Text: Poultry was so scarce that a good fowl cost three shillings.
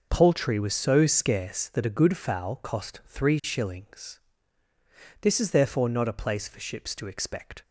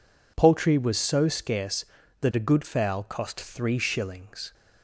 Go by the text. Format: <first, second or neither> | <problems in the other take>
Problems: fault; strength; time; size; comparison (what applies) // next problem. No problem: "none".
second | goes on to say "This is therefore not a place for ships to expect"; strong; from 5.2 s on; 2.4 s long